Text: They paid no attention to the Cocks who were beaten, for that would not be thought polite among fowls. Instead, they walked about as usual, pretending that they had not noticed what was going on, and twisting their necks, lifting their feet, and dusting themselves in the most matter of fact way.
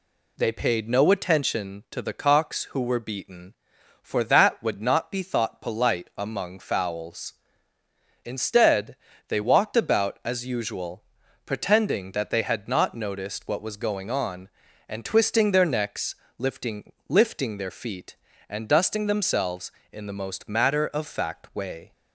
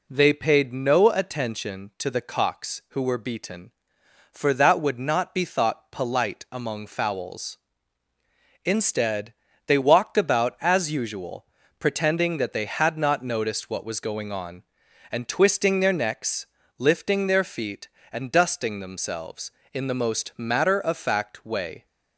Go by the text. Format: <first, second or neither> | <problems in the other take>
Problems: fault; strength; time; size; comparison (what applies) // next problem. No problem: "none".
second | says "lifting" twice; at 17.0 s